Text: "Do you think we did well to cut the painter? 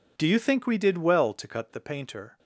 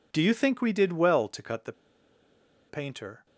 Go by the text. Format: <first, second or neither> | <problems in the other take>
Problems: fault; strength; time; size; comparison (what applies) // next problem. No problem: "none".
first | pauses between "the" and "painter"; noticeable; at 1.7 s; 0.96 s long